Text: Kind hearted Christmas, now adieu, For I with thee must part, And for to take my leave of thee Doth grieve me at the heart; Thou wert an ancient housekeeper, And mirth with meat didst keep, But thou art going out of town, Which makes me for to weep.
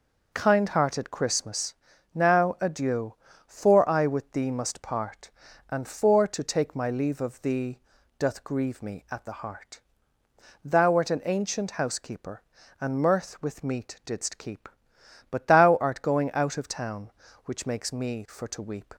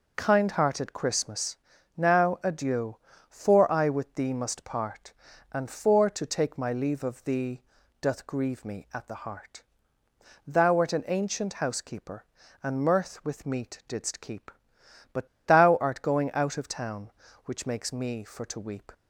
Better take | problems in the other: first | pauses between "thee" and "Doth"; at 7.6 s; 0.38 s long; also in the first // pauses between "But" and "thou"; slight; at 15.2 s; 0.18 s long

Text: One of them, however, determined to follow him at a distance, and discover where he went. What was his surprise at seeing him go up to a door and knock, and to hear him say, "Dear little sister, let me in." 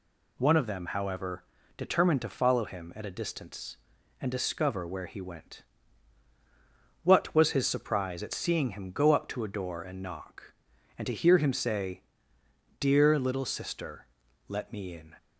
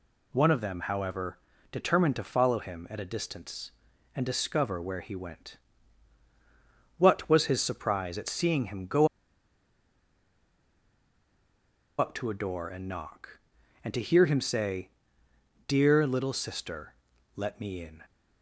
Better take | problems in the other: first | pauses between "go" and "up"; strong; at 9.0 s; 2.9 s long

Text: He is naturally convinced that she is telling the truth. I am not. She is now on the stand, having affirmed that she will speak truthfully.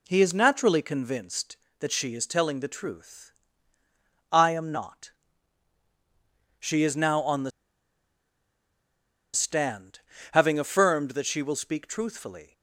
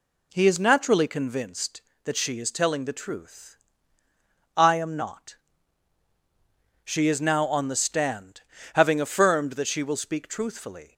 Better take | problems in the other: second | pauses between "the" and "stand"; strong; at 7.5 s; 1.8 s long

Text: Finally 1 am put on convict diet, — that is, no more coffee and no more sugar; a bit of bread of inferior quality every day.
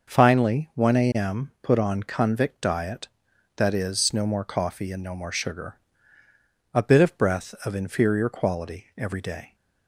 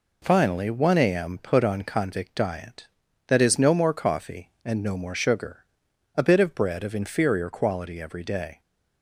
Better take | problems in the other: second | says "breath" for "bread"; at 7.1 s

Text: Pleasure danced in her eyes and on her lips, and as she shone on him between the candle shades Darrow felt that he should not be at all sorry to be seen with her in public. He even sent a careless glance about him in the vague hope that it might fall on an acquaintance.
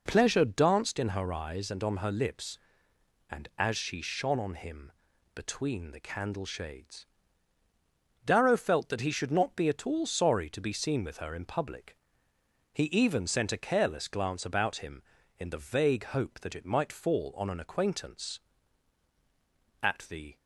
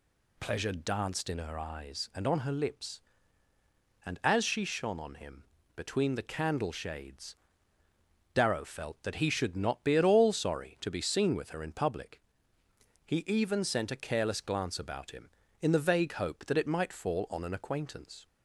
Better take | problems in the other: second | pauses between "him" and "between"; at 4.9 s; 0.42 s long; slight in the second // pauses between "shades" and "Darrow"; at 7.0 s; 1.2 s long; also in the second // goes on to say "At the"; from 19.8 s on; 0.56 s long

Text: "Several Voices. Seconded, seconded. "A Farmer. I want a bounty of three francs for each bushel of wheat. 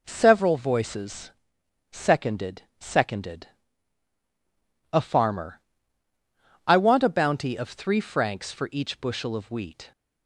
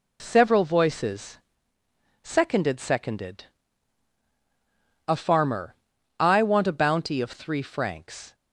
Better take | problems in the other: first | stops before "for each bushel of wheat"; at 8.3 s

